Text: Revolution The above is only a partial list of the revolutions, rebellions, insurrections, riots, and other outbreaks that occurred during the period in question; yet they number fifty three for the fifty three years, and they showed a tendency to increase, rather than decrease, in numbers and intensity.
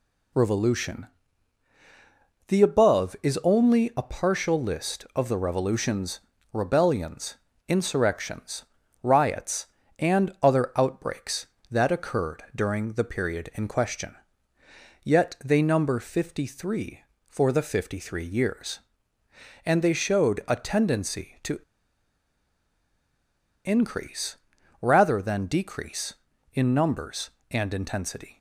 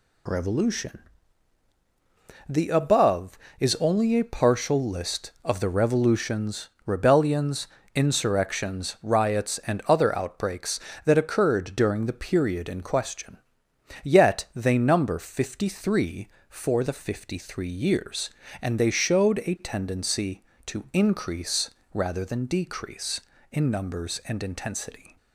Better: second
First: pauses between "Revolution" and "The"; strong; at 1.0 s; 1.4 s long // pauses between "to" and "increase"; strong; at 21.5 s; 2.0 s long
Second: pauses between "Revolution" and "The"; strong; at 0.9 s; 1.5 s long

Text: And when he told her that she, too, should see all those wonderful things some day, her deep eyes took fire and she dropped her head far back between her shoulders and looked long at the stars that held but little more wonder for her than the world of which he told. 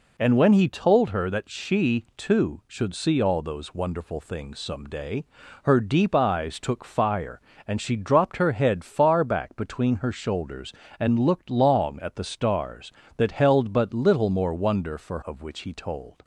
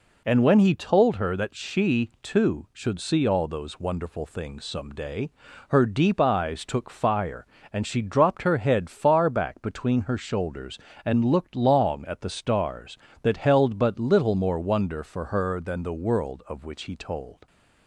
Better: second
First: skips "her than the world"; at 15.2 s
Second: none

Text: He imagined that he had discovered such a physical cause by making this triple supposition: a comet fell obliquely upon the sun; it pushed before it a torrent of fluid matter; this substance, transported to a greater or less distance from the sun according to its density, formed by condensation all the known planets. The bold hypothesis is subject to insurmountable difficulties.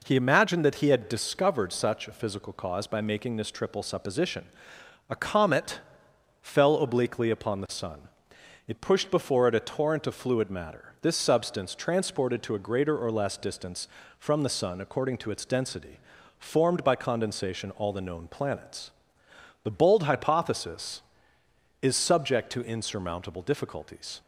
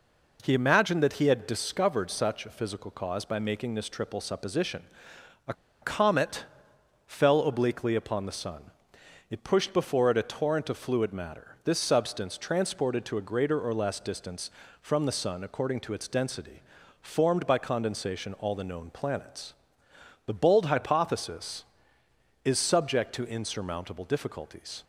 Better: first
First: pauses between "comet" and "fell"; noticeable; at 5.7 s; 0.62 s long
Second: pauses between "a" and "comet"; slight; at 5.5 s; 0.29 s long // pauses between "comet" and "fell"; noticeable; at 6.4 s; 0.62 s long

